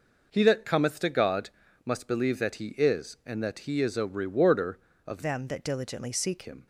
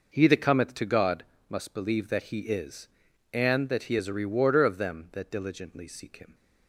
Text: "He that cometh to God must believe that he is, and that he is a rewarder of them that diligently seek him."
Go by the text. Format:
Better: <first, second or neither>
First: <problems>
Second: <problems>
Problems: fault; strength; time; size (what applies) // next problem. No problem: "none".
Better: second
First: pauses between "God" and "must"; slight; at 1.4 s; 0.36 s long // changes voice from "them" to "seek"; from 5.2 to 6.4 s; 1.2 s long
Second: pauses between "God" and "must"; slight; at 1.2 s; 0.24 s long